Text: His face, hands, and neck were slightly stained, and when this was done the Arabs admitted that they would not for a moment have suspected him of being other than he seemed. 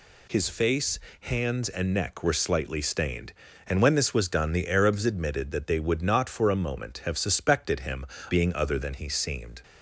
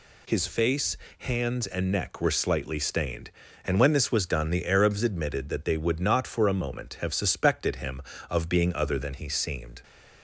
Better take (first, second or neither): second